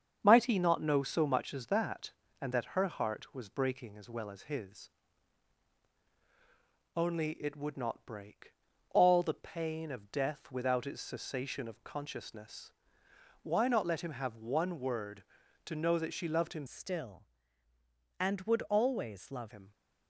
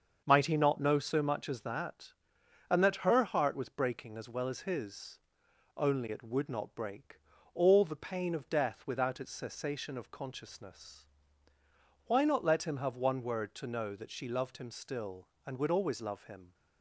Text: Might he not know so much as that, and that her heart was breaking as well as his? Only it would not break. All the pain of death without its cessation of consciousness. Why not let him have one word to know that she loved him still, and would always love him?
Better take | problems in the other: second | starts louder than the rest; strong; until 1.2 s; 7.5 dB; also in the second // changes voice from "still" to "love"; from 16.6 to 19.5 s; 2.9 s long

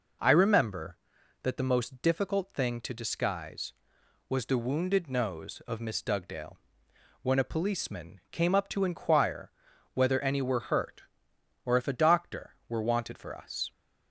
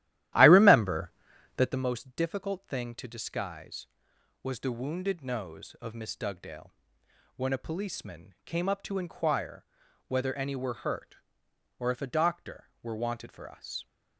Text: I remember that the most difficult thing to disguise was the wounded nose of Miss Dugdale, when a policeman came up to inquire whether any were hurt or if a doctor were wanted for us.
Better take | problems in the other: first | starts louder than the rest; strong; until 1.8 s; 13.5 dB // pauses between "inquire" and "whether"; at 9.6 s; 0.44 s long; also in the first

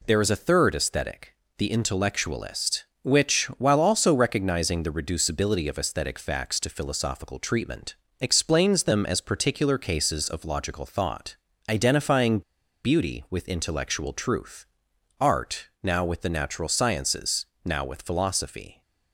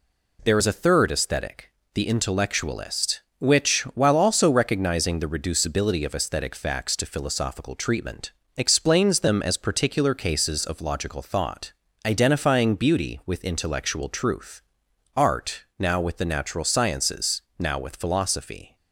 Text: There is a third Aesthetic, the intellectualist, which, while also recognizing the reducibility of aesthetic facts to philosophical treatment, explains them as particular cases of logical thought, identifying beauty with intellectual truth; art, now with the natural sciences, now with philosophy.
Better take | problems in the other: second | pauses between "identifying" and "beauty"; at 12.4 s; 0.43 s long

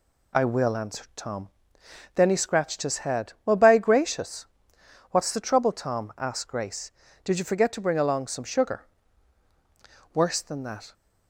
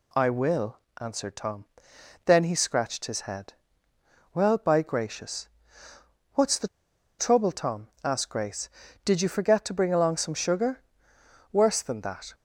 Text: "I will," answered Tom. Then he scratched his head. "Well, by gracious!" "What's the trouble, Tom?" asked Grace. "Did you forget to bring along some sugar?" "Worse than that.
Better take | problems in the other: first | pauses between "the" and "trouble"; noticeable; at 6.6 s; 0.50 s long

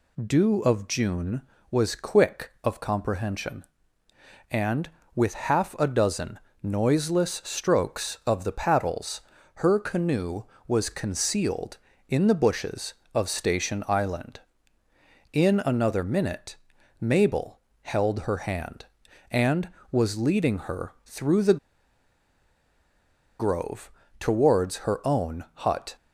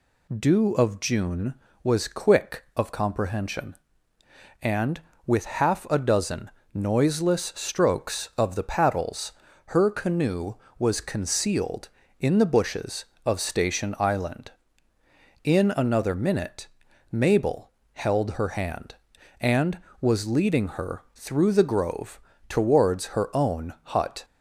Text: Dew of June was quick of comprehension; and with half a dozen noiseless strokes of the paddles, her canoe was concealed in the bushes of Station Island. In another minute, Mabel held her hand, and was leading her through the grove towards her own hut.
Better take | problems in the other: second | pauses between "dozen" and "noiseless"; slight; at 6.3 s; 0.24 s long; slight in the second // pauses between "Mabel" and "held"; slight; at 17.5 s; 0.24 s long; slight in the second // pauses between "the" and "grove"; strong; at 21.5 s; 1.8 s long // pauses between "grove" and "towards"; slight; at 23.9 s; 0.26 s long; slight in the second

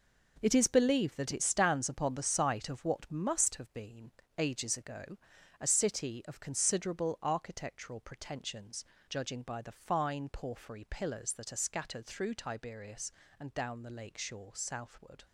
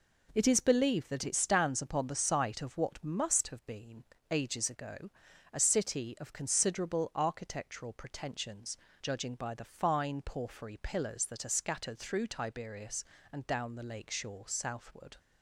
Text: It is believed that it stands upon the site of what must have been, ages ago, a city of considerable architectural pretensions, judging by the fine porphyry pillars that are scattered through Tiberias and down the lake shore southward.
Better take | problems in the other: second | gets quieter; strong; throughout; 9 dB

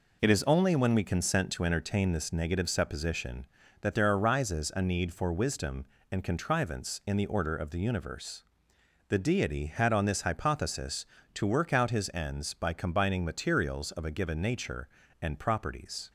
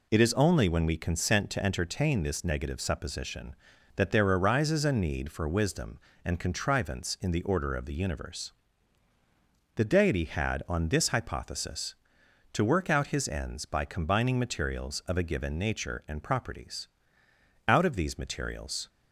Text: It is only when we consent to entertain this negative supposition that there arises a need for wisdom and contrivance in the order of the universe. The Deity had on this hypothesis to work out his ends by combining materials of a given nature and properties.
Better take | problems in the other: first | goes on to say "Out of these materials"; noticeable; from 17.6 s on; 1.2 s long

